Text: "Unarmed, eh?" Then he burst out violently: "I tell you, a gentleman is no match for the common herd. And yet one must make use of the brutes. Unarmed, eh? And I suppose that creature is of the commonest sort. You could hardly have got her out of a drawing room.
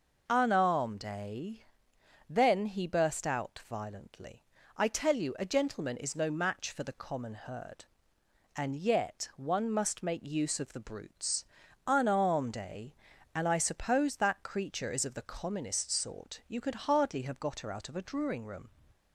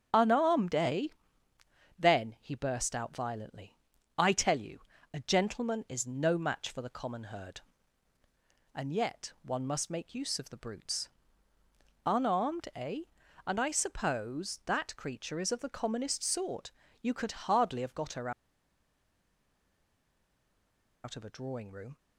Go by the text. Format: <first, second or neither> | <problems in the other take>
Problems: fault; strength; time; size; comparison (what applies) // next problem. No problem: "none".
first | starts louder than the rest; strong; until 2.0 s; 7.5 dB // pauses between "her" and "out"; strong; at 18.3 s; 2.7 s long